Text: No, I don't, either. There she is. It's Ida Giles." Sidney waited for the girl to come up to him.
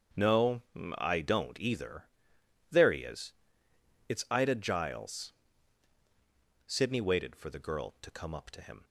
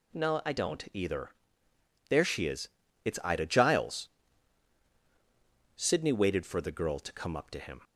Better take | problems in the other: second | starts louder than the rest; strong; until 1.5 s; 7.5 dB // says "he" for "she"; at 2.9 s

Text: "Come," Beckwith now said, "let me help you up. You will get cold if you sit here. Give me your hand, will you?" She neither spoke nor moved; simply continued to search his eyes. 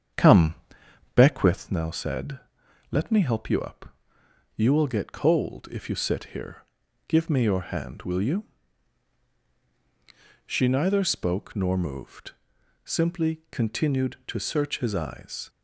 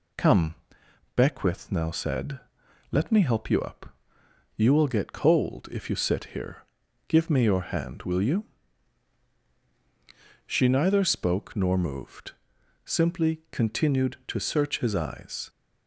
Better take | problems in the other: second | starts louder than the rest; strong; until 1.8 s; 8 dB

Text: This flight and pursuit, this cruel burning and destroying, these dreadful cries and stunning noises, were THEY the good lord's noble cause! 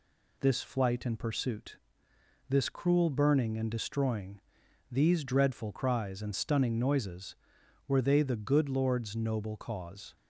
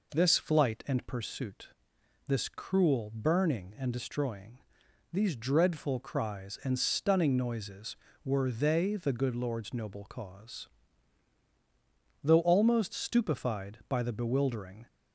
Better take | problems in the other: first | goes on to say "Though almost stupefied by the bewildering"; strong; from 12.2 s on; 2.6 s long

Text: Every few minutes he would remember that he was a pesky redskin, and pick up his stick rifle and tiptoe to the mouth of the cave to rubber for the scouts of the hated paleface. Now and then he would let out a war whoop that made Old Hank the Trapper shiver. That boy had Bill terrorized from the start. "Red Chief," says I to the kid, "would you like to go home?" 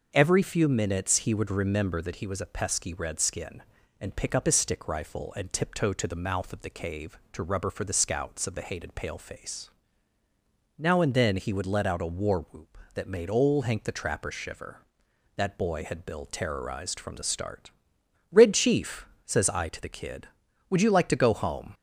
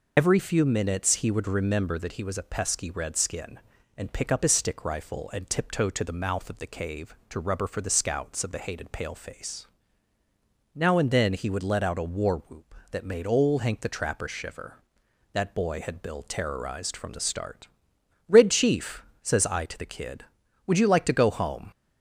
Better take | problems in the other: first | loses the start of "Every"; at 0.1 s; 65 ms

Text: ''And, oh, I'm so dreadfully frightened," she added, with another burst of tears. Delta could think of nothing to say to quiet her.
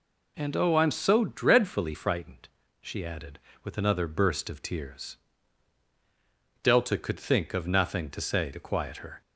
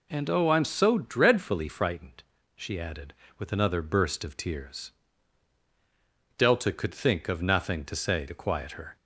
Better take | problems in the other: neither | none

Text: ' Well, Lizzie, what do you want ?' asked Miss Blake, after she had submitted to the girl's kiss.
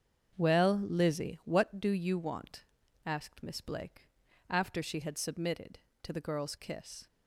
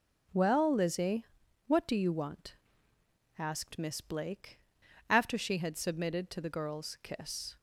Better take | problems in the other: second | starts louder than the rest; strong; until 1.8 s; 7.5 dB

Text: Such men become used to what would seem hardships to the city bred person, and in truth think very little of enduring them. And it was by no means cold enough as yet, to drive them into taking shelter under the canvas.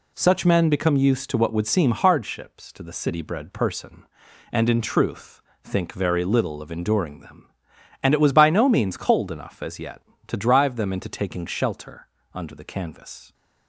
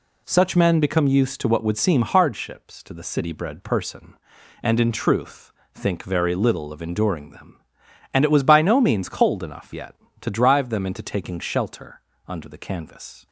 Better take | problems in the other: first | pauses between "truth" and "think"; slight; at 5.5 s; 0.24 s long; slight in the first // skips "as"; at 9.7 s // pauses between "shelter" and "under"; slight; at 12.0 s; 0.26 s long; slight in the first

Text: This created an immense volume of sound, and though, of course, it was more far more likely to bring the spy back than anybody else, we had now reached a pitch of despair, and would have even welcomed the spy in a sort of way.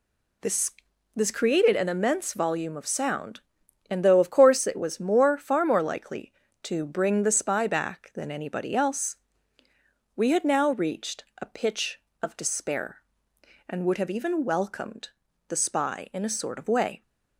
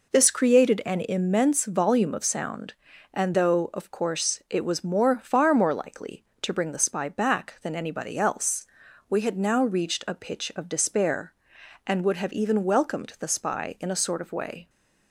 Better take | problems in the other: second | says "This" twice; at 1.1 s // pauses between "reached" and "a"; slight; at 11.2 s; 0.18 s long // pauses between "welcomed" and "the"; at 15.0 s; 0.40 s long

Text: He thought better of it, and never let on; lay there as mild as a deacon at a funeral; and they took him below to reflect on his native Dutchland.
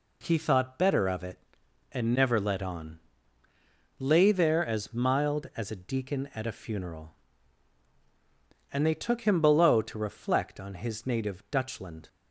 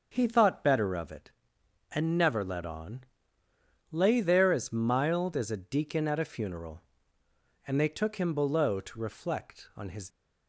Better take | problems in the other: first | starts louder than the rest; until 1.1 s; 6.5 dB // stops before "native Dutchland"; at 10.1 s

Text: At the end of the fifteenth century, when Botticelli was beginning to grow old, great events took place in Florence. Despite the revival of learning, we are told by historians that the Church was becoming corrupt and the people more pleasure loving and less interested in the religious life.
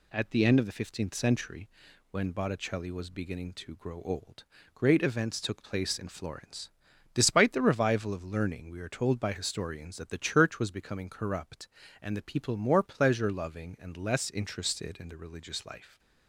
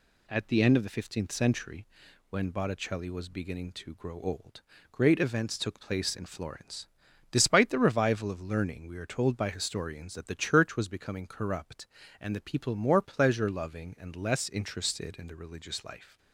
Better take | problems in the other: neither | none

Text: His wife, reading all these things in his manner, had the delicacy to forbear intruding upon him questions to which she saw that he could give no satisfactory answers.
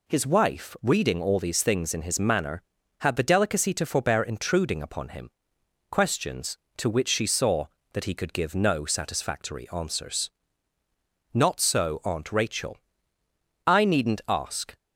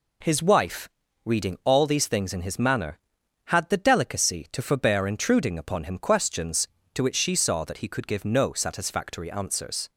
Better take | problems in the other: second | pauses between "him" and "questions"; noticeable; at 5.3 s; 0.60 s long // goes on to say "Not so Aunt Rachel I needn't ask"; strong; from 11.3 s on; 3.4 s long

